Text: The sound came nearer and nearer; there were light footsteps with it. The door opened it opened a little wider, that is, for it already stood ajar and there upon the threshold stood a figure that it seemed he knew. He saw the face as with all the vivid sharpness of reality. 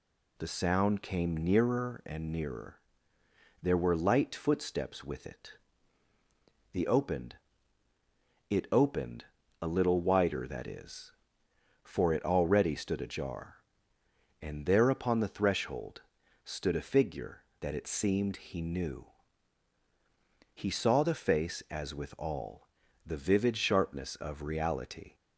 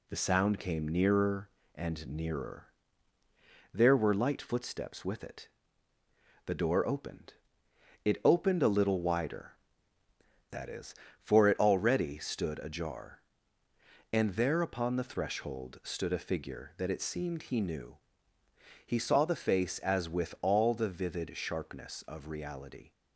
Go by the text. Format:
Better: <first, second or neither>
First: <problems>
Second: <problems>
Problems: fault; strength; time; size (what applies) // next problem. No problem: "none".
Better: second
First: skips "door"; at 6.8 s // pauses between "opened" and "it"; at 7.3 s; 1.1 s long // pauses between "opened" and "a"; slight; at 9.2 s; 0.36 s long // pauses between "threshold" and "stood"; at 16.0 s; 0.42 s long // pauses between "all" and "the"; at 22.6 s; 0.38 s long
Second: pauses between "opened" and "it"; noticeable; at 7.3 s; 0.72 s long